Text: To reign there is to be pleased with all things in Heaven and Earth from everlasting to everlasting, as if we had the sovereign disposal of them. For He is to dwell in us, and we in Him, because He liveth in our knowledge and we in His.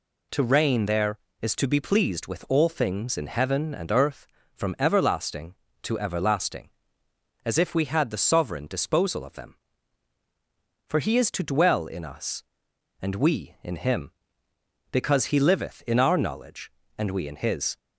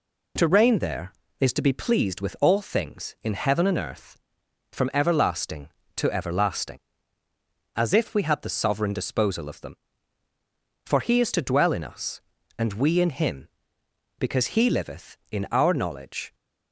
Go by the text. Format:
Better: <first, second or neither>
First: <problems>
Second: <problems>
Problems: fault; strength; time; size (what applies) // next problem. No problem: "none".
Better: first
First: none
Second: stops before "and we in His"; at 16.3 s